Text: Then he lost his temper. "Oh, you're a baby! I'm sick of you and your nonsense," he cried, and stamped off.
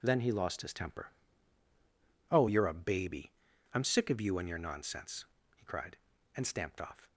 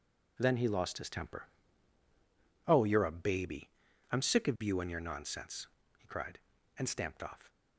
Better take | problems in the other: neither | none

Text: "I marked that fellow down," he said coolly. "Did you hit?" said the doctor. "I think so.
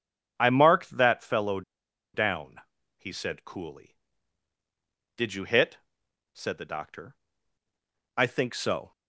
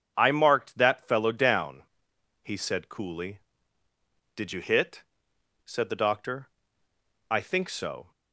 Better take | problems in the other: second | pauses between "fellow" and "down"; noticeable; at 1.6 s; 0.52 s long

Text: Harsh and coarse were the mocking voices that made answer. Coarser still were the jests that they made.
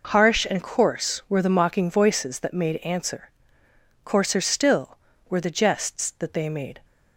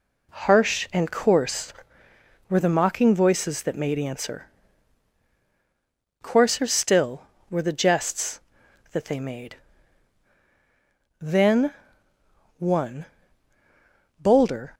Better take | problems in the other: first | goes on to say "Then one bolder"; strong; from 11.1 s on; 3.5 s long

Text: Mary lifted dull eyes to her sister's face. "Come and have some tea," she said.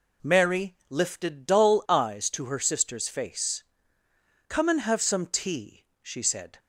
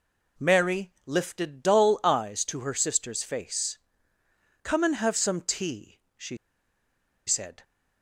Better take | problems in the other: first | pauses between "she" and "said"; noticeable; at 6.3 s; 0.89 s long

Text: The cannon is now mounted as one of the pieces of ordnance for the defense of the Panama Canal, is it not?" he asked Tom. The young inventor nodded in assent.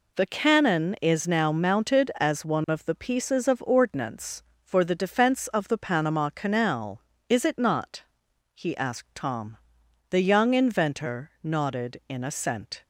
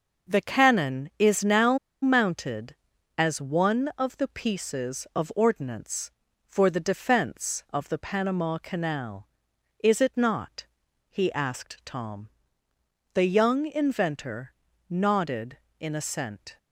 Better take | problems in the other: first | starts louder than the rest; noticeable; until 1.3 s; 6 dB // pauses between "now" and "mounted"; slight; at 1.7 s; 0.24 s long // pauses between "inventor" and "nodded"; at 14.5 s; 0.38 s long

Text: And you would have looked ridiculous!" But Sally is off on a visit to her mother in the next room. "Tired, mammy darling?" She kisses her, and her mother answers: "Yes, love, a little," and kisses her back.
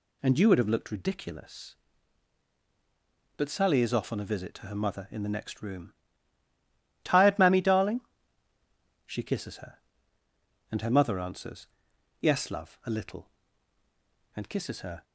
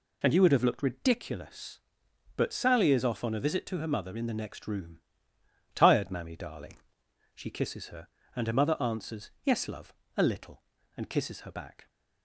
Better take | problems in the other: second | stops before "back"; at 15.0 s

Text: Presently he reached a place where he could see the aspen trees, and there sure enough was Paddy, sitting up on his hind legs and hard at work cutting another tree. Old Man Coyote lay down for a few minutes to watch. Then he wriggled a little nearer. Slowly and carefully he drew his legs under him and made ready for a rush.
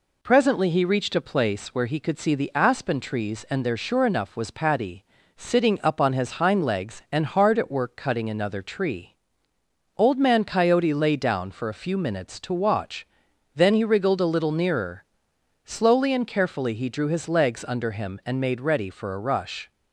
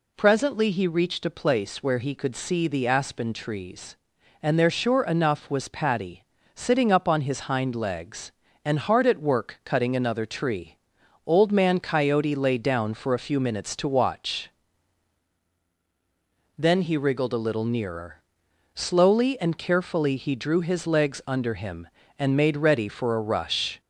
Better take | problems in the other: first | gets louder; slight; throughout; 2.5 dB

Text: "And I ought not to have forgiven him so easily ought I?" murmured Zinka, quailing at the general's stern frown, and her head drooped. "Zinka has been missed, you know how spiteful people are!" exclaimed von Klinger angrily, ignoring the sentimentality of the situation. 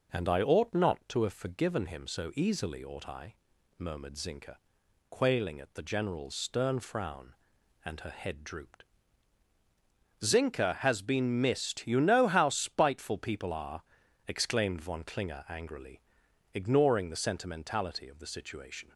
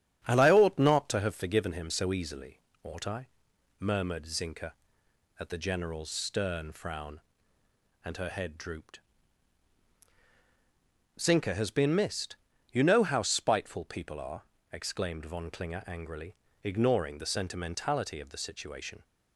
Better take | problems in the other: first | starts louder than the rest; strong; until 1.2 s; 8.5 dB // pauses between "easily" and "ought"; slight; at 2.6 s; 0.20 s long // skips "quailing"; at 5.0 s

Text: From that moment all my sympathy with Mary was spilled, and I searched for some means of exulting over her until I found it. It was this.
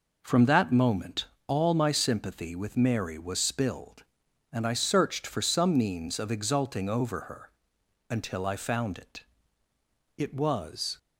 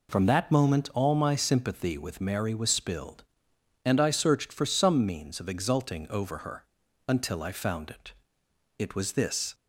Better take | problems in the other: second | pauses between "moment" and "all"; slight; at 1.2 s; 0.22 s long // pauses between "her" and "until"; noticeable; at 7.4 s; 0.60 s long; also in the second // stops before "this"; at 10.9 s

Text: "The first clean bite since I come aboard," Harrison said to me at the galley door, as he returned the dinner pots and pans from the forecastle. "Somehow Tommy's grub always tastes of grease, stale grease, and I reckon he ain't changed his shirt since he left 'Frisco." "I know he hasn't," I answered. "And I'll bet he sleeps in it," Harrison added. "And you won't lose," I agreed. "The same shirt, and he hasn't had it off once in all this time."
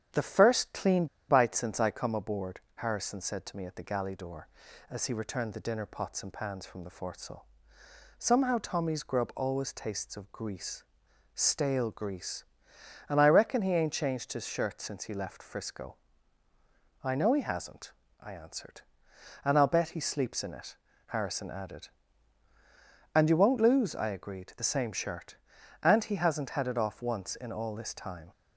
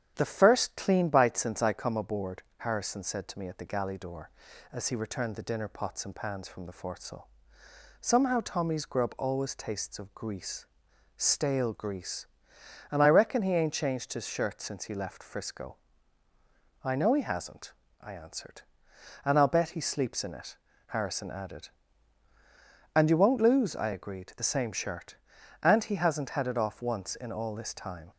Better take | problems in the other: second | starts louder than the rest; strong; until 1.3 s; 9.5 dB; strong in the second // pauses between "clean" and "bite"; slight; at 1.0 s; 0.23 s long

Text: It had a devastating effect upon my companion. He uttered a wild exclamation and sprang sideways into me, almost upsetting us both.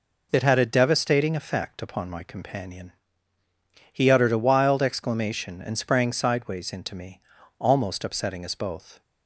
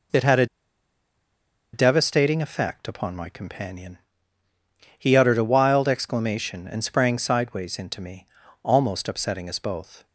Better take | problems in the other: first | pauses between "a" and "devastating"; strong; at 0.4 s; 1.2 s long

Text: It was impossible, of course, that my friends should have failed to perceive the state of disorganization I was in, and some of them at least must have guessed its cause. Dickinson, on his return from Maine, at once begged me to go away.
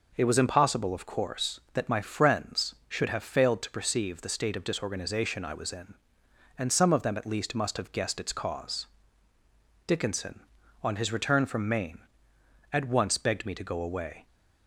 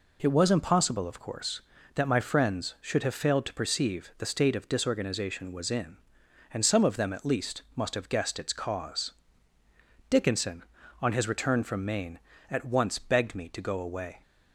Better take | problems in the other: first | skips "I"; at 5.5 s

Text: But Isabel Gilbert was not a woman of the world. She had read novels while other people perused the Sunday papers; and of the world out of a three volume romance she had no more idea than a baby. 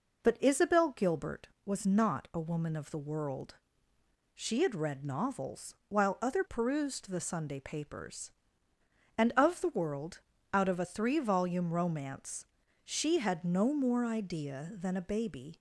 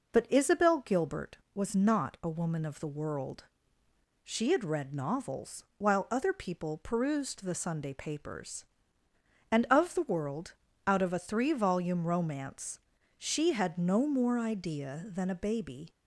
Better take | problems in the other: second | skips "people"; at 6.4 s // pauses between "world" and "out"; slight; at 10.2 s; 0.32 s long; slight in the second // pauses between "romance" and "she"; at 12.4 s; 0.40 s long; also in the second

